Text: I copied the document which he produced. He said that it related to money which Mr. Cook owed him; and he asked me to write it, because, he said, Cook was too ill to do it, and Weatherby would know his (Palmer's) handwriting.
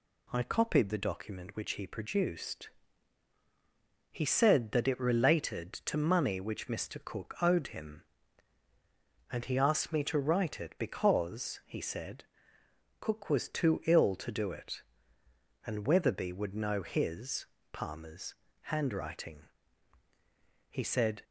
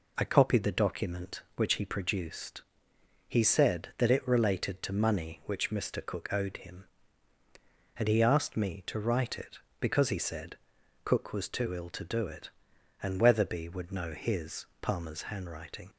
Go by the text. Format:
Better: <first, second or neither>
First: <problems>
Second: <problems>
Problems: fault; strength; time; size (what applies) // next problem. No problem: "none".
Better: second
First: goes on to say "He said"; from 20.6 s on; 0.54 s long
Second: none